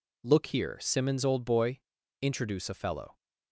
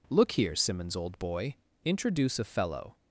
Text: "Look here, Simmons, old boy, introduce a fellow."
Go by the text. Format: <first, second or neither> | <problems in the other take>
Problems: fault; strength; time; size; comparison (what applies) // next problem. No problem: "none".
neither | none